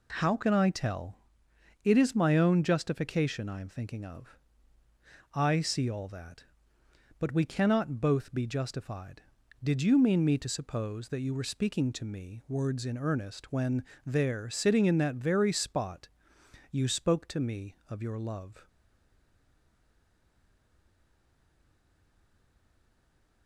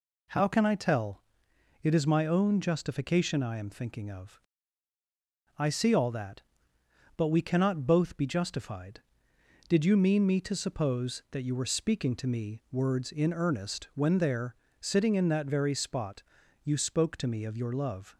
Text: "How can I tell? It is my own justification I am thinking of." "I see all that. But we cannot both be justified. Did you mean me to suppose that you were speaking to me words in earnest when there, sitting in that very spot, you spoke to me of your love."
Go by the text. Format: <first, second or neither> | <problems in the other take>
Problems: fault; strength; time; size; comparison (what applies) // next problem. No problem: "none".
second | pauses between "when" and "there"; slight; at 13.8 s; 0.20 s long // stays silent after the last word; strong; from 18.6 s on; 4.8 s long